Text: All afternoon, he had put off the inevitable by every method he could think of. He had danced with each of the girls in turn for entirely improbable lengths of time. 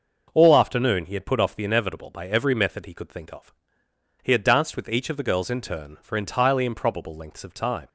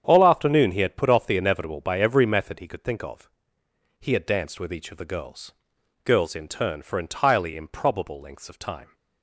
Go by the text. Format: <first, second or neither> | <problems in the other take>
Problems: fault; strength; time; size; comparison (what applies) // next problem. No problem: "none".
first | starts louder than the rest; strong; until 1.0 s; 8.5 dB // says "girls" twice; at 6.0 s